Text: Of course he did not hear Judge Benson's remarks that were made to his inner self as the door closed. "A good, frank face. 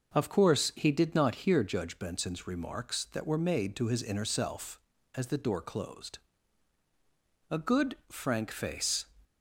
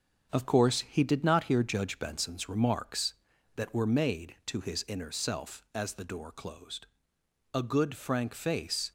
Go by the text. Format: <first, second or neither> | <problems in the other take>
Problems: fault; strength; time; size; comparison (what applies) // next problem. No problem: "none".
first | gets quieter; noticeable; throughout; 5 dB